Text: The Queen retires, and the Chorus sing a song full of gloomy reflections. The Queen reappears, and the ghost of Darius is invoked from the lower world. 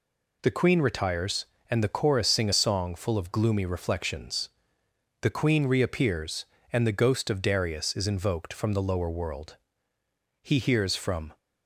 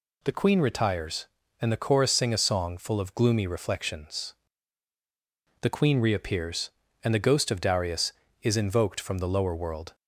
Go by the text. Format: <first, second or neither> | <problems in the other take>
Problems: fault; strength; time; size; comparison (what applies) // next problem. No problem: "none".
second | goes on to say "He hears from"; noticeable; from 10.4 s on; 0.94 s long